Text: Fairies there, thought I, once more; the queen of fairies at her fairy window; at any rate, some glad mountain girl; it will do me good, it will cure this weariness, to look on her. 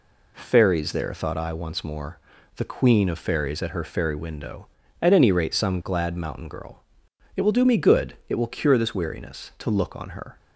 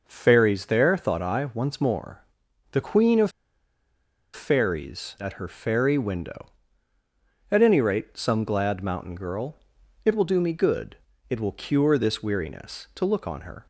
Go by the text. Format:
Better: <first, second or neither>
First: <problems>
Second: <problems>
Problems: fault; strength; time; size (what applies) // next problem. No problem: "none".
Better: first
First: none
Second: pauses between "of" and "fairies"; at 3.2 s; 1.0 s long